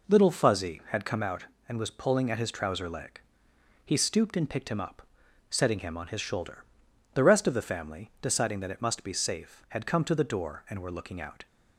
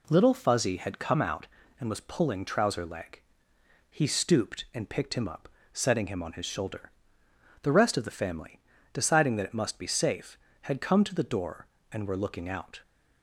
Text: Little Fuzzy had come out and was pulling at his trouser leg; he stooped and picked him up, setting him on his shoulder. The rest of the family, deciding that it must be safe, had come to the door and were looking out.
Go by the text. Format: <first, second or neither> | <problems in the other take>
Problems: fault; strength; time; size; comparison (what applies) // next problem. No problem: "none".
first | skips "at his"; at 2.4 s